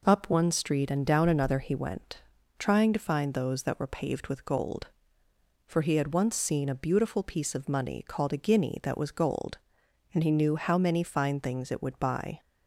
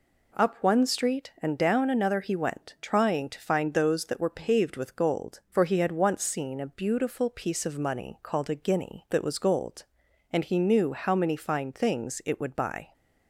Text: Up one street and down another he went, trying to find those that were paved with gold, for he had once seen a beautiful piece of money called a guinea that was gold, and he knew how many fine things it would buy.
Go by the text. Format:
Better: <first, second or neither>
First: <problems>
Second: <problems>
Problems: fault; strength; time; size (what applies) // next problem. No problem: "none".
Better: neither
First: none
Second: none